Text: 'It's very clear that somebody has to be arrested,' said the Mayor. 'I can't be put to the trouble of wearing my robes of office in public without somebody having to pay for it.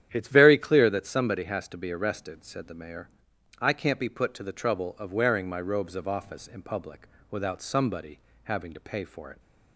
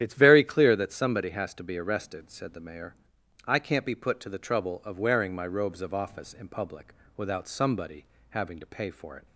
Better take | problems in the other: first | loses the start of "It's"; at 0.0 s; 30 ms // starts louder than the rest; strong; until 1.0 s; 10 dB; strong in the first // pauses between "public" and "without"; slight; at 6.9 s; 0.22 s long; slight in the first // pauses between "somebody" and "having"; slight; at 8.0 s; 0.24 s long; slight in the first

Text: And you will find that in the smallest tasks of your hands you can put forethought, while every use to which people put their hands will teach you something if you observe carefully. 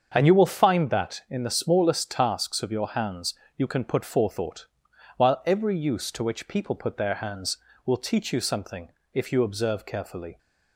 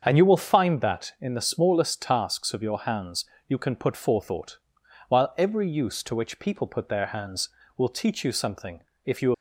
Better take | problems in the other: first | starts louder than the rest; until 1.0 s; 7 dB; also in the first // pauses between "hands" and "you"; slight; at 3.2 s; 0.24 s long; slight in the first // pauses between "something" and "if"; slight; at 8.8 s; 0.24 s long; slight in the first // stops before "observe carefully"; at 9.3 s

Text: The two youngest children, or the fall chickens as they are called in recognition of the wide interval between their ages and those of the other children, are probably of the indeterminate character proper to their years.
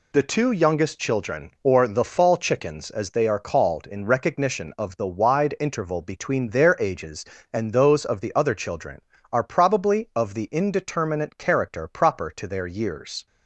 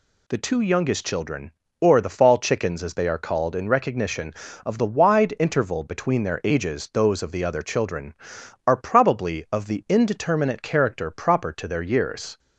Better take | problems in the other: first | skips "and"; at 6.9 s

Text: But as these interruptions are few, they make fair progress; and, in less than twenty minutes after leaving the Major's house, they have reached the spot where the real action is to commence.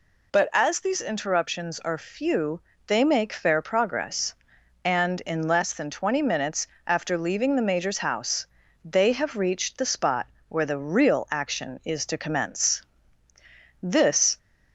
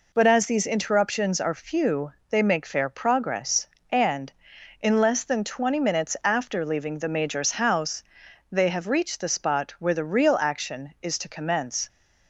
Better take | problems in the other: second | pauses between "minutes" and "after"; slight; at 6.6 s; 0.22 s long // pauses between "spot" and "where"; slight; at 10.2 s; 0.22 s long // goes on to say "This"; from 13.7 s on; 0.58 s long

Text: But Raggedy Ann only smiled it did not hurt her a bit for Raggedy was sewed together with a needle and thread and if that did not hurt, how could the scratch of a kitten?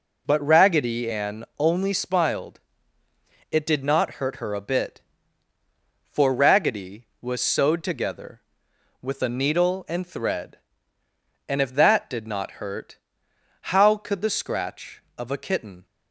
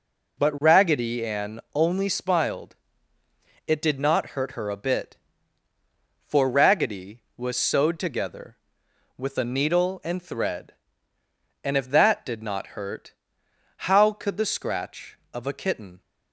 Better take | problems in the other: neither | pauses between "smiled" and "it"; noticeable; the same in both

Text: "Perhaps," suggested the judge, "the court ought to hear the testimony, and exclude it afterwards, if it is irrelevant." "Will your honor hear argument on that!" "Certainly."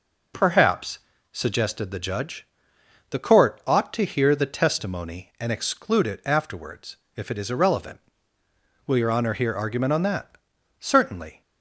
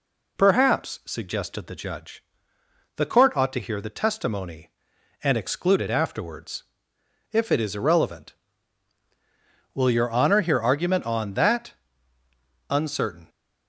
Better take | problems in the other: first | says "Uncertain" for "Certainly"; at 12.6 s

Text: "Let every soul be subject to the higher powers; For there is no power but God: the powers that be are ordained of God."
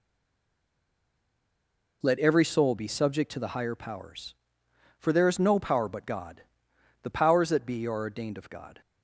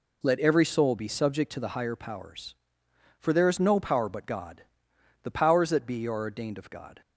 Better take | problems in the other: second | stays silent before the first word; noticeable; until 2.0 s; 2.0 s long

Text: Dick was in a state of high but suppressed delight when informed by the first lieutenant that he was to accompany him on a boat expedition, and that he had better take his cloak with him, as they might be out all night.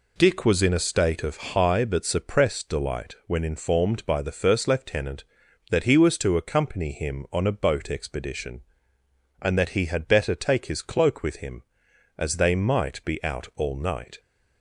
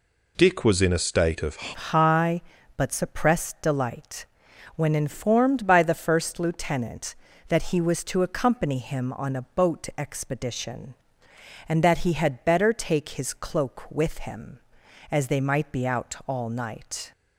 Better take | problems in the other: first | changes voice at "high"; from 1.7 s on; 15.4 s long // pauses between "delight" and "when"; noticeable; at 4.2 s; 0.50 s long

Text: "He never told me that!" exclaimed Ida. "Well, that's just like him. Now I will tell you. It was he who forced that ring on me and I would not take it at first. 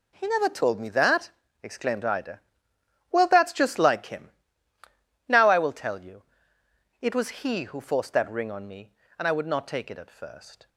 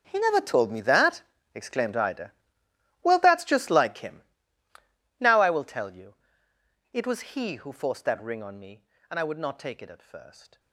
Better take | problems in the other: first | gets quieter; strong; throughout; 16.5 dB

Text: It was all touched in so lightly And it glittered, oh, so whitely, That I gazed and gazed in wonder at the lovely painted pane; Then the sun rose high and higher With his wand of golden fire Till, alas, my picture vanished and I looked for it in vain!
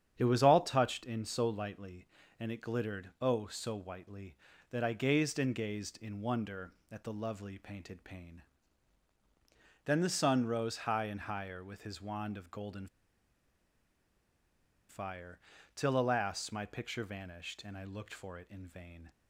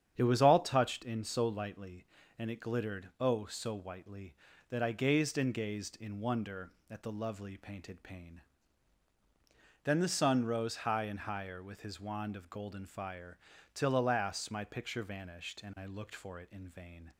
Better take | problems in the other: second | starts louder than the rest; strong; until 1.1 s; 8.5 dB; strong in the second // pauses between "golden" and "fire"; strong; at 12.8 s; 2.0 s long // pauses between "fire" and "Till"; slight; at 15.3 s; 0.36 s long; slight in the second

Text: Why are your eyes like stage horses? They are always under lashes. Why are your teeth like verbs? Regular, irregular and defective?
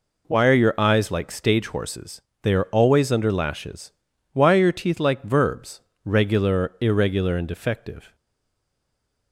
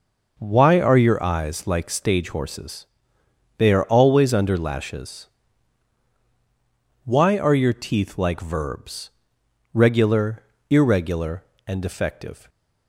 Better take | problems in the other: second | stays silent after the last word; noticeable; from 8.1 s on; 1.2 s long

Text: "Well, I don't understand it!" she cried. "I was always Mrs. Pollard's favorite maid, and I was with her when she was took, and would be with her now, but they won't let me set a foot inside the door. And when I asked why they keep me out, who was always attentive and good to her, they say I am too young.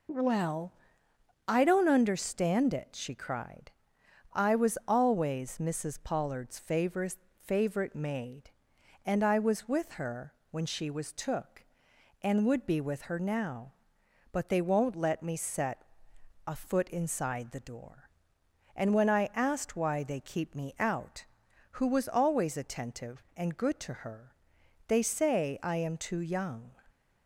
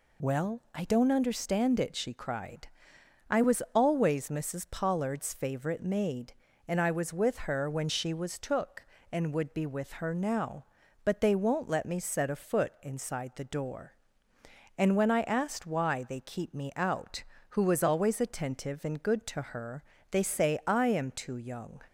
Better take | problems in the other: second | says "favorite" twice; at 7.4 s // pauses between "her" and "when"; slight; at 10.3 s; 0.18 s long // pauses between "set" and "a"; noticeable; at 15.8 s; 0.62 s long

